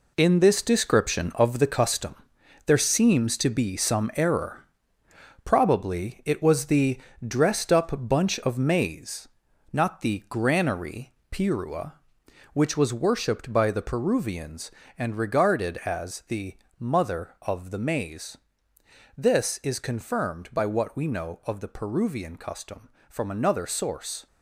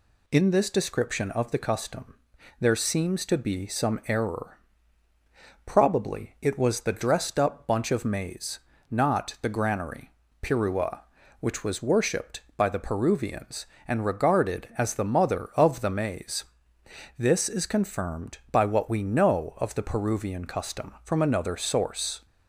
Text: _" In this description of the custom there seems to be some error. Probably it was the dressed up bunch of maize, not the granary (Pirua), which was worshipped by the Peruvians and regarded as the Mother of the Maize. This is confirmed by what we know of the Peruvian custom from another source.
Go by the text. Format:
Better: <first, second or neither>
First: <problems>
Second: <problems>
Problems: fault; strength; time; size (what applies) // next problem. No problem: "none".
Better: second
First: gets quieter; strong; throughout; 9 dB // pauses between "custom" and "there"; noticeable; at 2.1 s; 0.52 s long // pauses between "the" and "dressed"; slight; at 7.0 s; 0.26 s long // pauses between "the" and "Mother"; slight; at 16.5 s; 0.22 s long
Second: pauses between "custom" and "there"; at 2.1 s; 0.44 s long